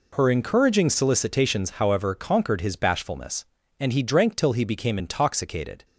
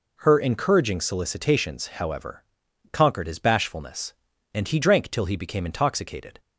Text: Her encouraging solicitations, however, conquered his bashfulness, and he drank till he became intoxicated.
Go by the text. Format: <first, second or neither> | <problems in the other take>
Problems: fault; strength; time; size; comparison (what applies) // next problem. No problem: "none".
neither | none